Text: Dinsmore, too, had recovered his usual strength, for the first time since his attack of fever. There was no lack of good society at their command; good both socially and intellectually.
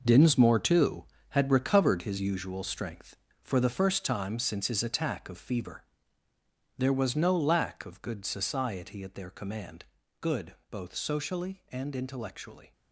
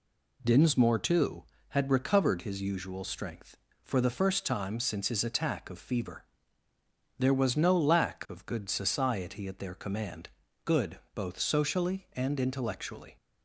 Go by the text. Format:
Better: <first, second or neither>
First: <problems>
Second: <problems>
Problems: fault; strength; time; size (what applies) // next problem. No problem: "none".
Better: second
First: gets quieter; strong; throughout; 10.5 dB // pauses between "good" and "both"; slight; at 10.5 s; 0.16 s long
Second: pauses between "good" and "both"; slight; at 10.9 s; 0.16 s long